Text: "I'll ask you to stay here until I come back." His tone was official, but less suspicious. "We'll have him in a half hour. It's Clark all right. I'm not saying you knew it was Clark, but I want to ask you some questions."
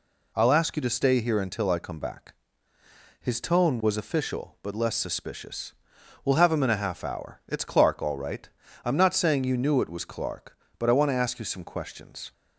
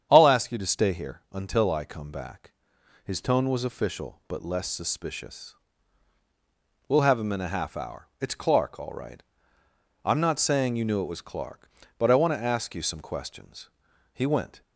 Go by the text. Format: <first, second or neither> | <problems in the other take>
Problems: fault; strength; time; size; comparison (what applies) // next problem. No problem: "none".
first | starts louder than the rest; strong; until 1.1 s; 8.5 dB // goes on to say "He went"; slight; from 14.1 s on; 0.48 s long